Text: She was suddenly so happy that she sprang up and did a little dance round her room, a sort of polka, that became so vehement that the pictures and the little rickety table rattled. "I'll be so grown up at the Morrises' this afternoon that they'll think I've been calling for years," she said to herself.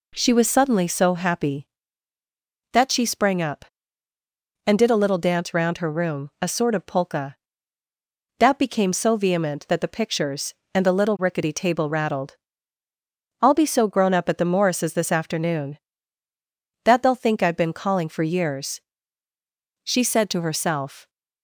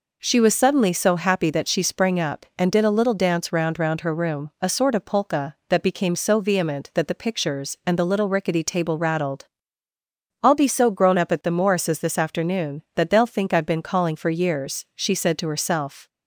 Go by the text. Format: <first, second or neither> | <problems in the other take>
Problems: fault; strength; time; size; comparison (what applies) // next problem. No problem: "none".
first | says "round" twice; at 3.7 s